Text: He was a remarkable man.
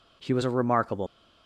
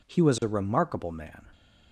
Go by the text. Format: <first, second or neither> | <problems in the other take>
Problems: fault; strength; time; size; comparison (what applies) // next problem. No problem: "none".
second | stops before "man"; at 1.0 s